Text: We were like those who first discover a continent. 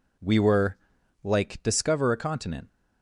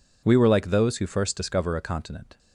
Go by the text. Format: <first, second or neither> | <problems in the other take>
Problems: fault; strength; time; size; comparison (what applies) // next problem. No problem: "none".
second | pauses between "were" and "like"; noticeable; at 0.7 s; 0.48 s long // skips "those who first"; at 1.6 s